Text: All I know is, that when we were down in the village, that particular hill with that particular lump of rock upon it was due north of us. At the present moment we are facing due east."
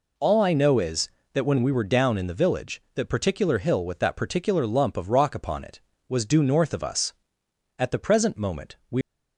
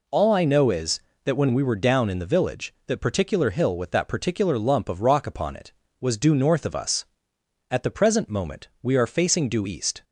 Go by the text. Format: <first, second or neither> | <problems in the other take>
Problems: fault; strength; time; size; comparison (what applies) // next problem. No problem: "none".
second | stops before "are facing due east"; at 9.0 s